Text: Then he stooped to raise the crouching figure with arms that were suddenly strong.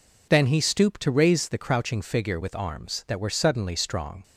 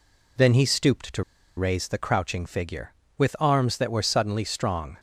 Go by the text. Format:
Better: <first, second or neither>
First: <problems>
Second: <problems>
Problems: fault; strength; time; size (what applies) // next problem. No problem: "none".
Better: first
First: none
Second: pauses between "to" and "raise"; slight; at 1.2 s; 0.33 s long